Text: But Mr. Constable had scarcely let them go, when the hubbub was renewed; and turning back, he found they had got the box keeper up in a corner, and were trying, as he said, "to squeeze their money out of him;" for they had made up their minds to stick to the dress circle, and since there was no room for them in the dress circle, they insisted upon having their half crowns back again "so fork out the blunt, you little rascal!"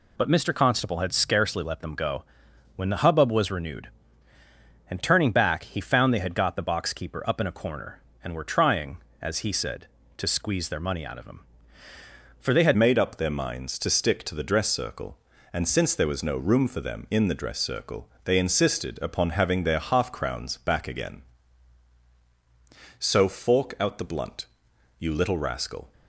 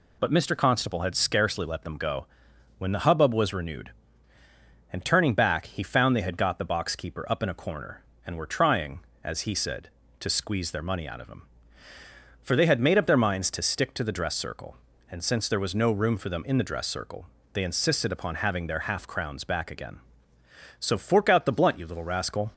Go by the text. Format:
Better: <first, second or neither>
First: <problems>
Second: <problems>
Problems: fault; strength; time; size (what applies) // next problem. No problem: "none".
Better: second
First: changes voice at "made"; from 12.7 s on; 13.2 s long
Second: none